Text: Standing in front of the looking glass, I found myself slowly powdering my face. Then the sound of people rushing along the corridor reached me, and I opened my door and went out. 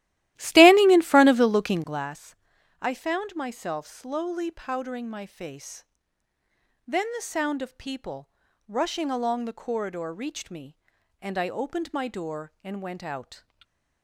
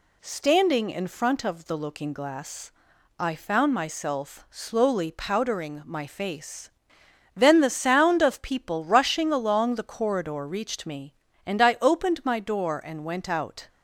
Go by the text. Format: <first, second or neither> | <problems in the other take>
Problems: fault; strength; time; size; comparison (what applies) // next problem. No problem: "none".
second | starts louder than the rest; strong; until 2.1 s; 15 dB // pauses between "people" and "rushing"; at 8.2 s; 0.38 s long // stays silent after the last word; slight; from 13.3 s on; 0.7 s long